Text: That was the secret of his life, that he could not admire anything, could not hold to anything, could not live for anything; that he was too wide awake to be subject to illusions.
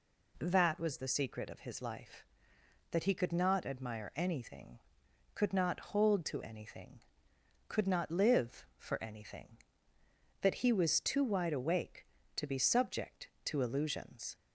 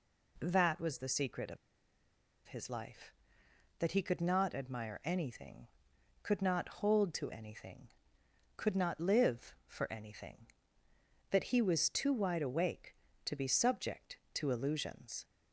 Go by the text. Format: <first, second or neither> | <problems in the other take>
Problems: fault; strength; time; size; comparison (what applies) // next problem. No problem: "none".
first | pauses between "of" and "his"; noticeable; at 1.5 s; 0.90 s long